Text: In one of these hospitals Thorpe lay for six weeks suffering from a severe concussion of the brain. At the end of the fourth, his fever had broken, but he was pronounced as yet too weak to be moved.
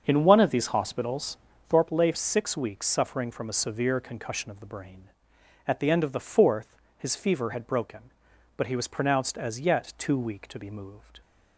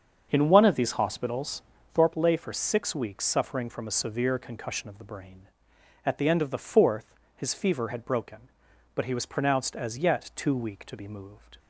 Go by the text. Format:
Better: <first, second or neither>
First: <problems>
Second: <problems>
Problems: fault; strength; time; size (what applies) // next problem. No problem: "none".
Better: second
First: starts louder than the rest; until 1.0 s; 7 dB // pauses between "hospitals" and "Thorpe"; slight; at 1.3 s; 0.32 s long // skips "for"; at 2.1 s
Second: starts louder than the rest; until 1.3 s; 7 dB // pauses between "hospitals" and "Thorpe"; slight; at 1.6 s; 0.32 s long